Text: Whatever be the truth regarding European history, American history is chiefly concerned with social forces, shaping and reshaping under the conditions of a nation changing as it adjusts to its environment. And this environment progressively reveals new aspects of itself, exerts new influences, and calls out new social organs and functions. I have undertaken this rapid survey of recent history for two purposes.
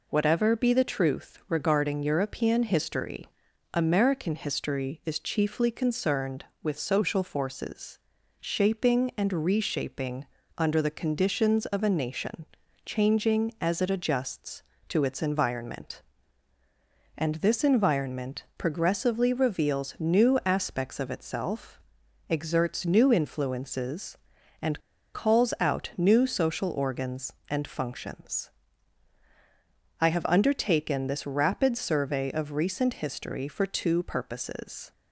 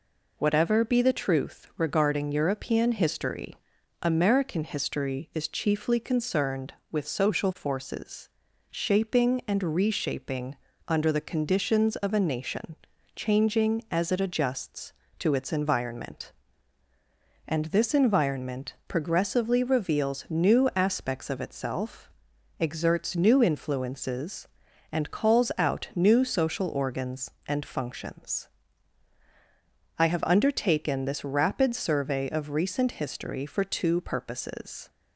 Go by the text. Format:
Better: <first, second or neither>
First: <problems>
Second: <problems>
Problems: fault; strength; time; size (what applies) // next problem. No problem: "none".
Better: second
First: pauses between "reshaping" and "under"; slight; at 10.2 s; 0.32 s long // pauses between "nation" and "changing"; at 12.4 s; 0.40 s long // pauses between "and" and "calls"; slight; at 24.7 s; 0.34 s long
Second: pauses between "reshaping" and "under"; slight; at 10.5 s; 0.32 s long // pauses between "nation" and "changing"; at 12.7 s; 0.40 s long